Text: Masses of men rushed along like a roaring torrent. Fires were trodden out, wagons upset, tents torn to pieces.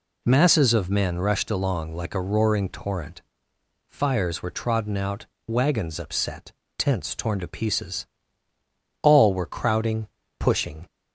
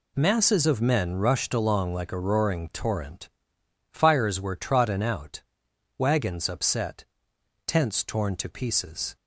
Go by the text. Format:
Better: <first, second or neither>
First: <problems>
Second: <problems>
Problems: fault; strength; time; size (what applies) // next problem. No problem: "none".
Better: second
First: goes on to say "All were crowding pushing"; strong; from 9.0 s on; 1.8 s long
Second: none